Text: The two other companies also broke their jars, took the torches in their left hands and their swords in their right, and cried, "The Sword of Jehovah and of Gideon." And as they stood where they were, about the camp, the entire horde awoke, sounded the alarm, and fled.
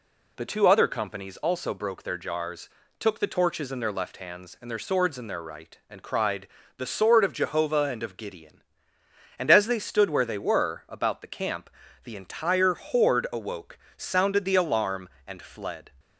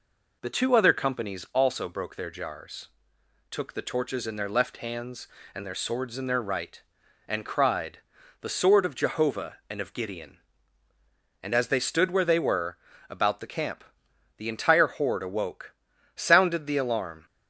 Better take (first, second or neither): first